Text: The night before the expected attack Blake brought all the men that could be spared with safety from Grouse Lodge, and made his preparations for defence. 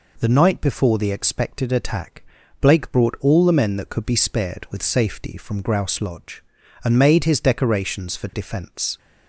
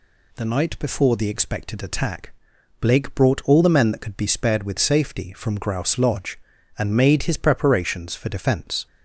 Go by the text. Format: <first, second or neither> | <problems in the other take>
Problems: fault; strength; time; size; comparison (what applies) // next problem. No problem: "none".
second | pauses between "attack" and "Blake"; at 2.2 s; 0.40 s long; noticeable in the second // says "decorations" for "preparations"; at 7.3 s